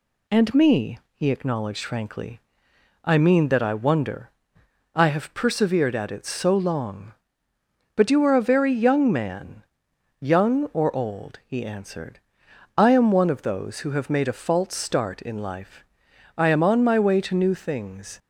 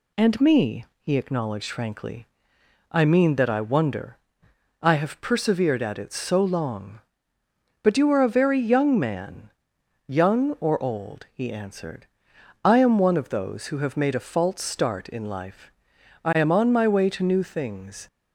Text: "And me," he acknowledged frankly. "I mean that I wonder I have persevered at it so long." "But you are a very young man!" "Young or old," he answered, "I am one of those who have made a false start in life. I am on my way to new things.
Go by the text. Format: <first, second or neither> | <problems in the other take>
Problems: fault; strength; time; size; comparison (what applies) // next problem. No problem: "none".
neither | pauses between "wonder" and "I"; noticeable; the same in both